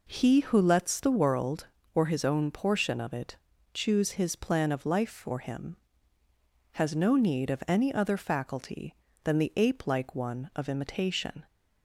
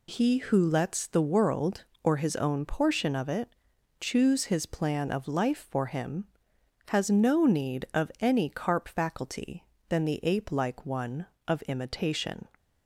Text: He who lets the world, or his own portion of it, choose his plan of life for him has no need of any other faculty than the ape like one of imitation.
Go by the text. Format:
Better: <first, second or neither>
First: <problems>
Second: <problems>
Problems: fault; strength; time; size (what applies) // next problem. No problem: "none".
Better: first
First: none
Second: says "carp" for "other"; at 8.4 s